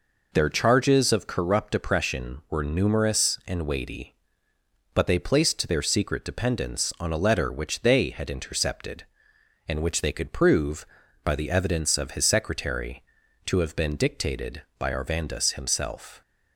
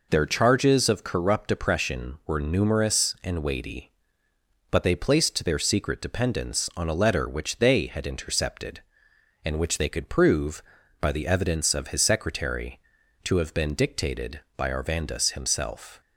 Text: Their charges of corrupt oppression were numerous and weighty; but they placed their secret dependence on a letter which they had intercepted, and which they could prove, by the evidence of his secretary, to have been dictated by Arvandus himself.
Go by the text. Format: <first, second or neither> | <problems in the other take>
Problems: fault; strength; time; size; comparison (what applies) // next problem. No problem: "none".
neither | none